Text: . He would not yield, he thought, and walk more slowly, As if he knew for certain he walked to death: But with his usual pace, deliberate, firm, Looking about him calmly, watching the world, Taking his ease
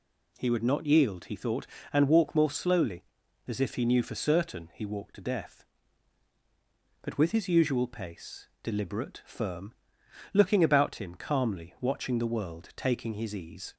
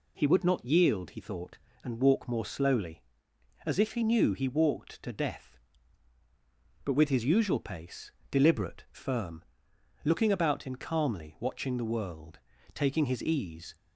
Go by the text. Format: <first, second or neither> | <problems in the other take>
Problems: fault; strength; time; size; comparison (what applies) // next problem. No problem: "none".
first | skips "for certain"; at 4.3 s